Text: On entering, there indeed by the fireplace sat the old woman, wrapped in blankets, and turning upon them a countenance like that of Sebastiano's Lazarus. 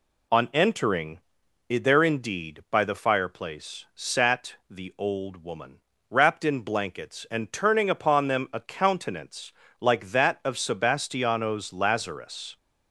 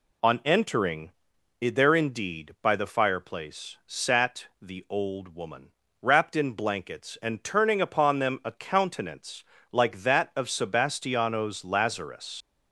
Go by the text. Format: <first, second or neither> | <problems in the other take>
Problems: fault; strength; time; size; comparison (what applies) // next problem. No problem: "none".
first | pauses between "countenance" and "like"; slight; at 9.4 s; 0.28 s long; slight in the first // leaves "Lazarus" unfinished; at 12.4 s; 75 ms